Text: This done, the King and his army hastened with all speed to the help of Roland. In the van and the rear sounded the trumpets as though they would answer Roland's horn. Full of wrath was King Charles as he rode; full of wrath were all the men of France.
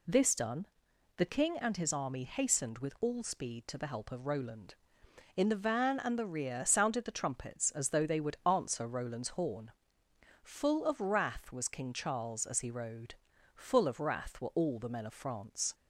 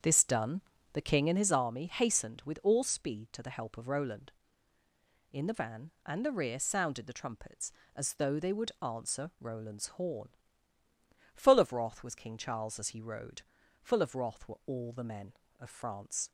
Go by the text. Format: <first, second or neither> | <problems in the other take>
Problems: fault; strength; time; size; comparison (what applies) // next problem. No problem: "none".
first | starts louder than the rest; strong; until 1.5 s; 7.5 dB